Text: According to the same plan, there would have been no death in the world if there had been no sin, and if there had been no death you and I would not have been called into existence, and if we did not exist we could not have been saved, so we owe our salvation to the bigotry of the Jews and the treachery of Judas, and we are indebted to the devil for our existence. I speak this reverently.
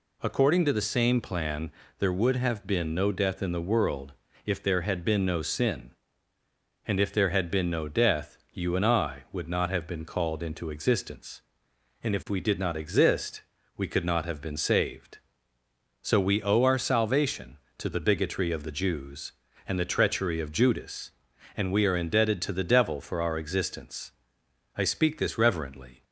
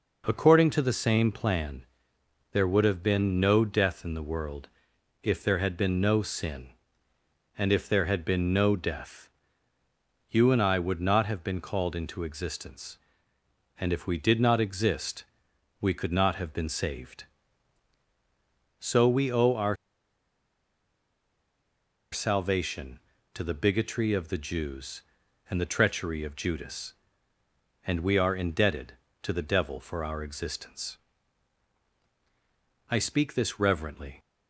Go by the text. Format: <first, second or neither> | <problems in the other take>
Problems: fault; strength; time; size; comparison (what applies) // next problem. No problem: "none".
first | pauses between "world" and "if"; noticeable; at 4.6 s; 0.52 s long; slight in the first // pauses between "death" and "you"; at 9.2 s; 1.0 s long // pauses between "exist" and "we"; noticeable; at 15.2 s; 0.56 s long; slight in the first // pauses between "our" and "salvation"; strong; at 19.7 s; 2.3 s long